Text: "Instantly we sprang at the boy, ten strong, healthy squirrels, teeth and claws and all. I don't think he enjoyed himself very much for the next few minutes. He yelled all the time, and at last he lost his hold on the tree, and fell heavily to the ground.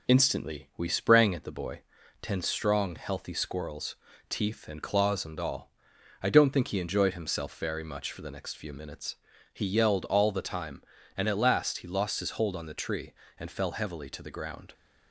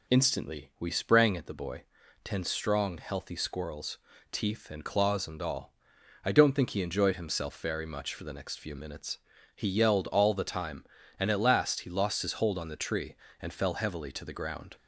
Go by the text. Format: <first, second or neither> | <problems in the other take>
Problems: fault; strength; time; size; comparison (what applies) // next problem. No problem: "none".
second | gets quieter; slight; throughout; 2 dB